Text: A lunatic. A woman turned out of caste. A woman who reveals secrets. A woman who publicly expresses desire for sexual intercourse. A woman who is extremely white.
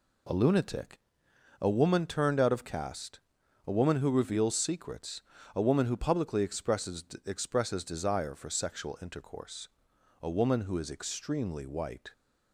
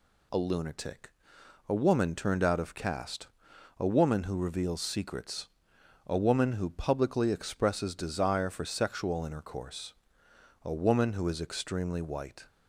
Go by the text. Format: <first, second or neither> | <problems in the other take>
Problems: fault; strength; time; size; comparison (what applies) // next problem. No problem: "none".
second | says "expresses" twice; at 7.2 s